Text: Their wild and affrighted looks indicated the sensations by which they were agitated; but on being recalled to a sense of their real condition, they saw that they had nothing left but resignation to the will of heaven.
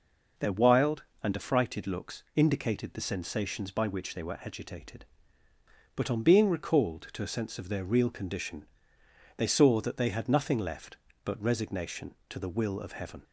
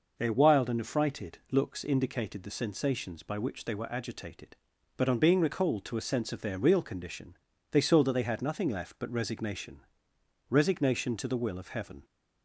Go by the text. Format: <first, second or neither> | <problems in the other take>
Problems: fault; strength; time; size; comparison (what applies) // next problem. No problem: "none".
first | says "resignation" twice; at 10.5 s